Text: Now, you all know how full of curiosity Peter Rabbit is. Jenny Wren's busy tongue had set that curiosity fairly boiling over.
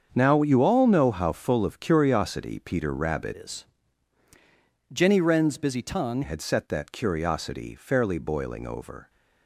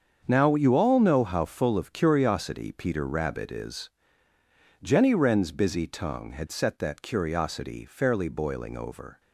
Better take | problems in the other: second | starts louder than the rest; until 1.1 s; 7 dB; strong in the second // changes voice from "is" to "tongue"; from 3.3 to 6.2 s; 2.9 s long

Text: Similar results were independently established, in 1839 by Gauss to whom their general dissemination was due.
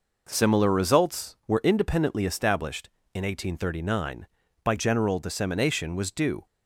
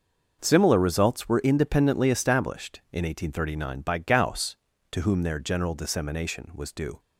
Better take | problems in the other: second | skips "Gauss to whom their"; at 4.7 s

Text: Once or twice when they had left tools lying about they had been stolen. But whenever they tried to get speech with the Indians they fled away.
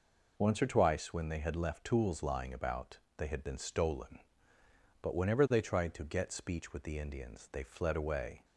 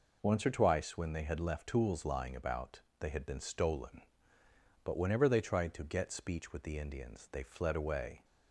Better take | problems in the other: neither | pauses between "about" and "they"; slight; the same in both

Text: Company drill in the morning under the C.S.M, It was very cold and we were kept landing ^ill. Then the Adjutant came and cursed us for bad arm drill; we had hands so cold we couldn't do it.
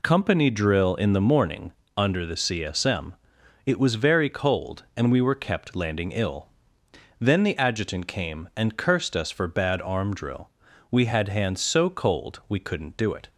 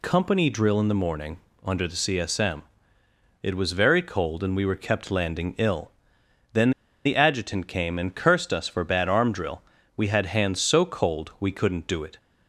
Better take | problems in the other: first | pauses between "morning" and "under"; slight; at 1.3 s; 0.24 s long; slight in the first // pauses between "Then" and "the"; slight; at 6.7 s; 0.33 s long

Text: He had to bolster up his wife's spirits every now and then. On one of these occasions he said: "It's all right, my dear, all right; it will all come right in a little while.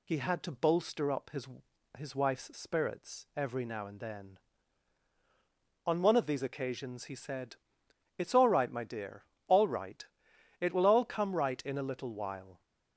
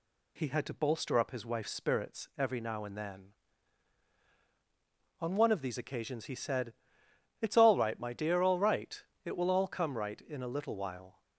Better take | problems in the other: second | says "his" twice; at 1.9 s

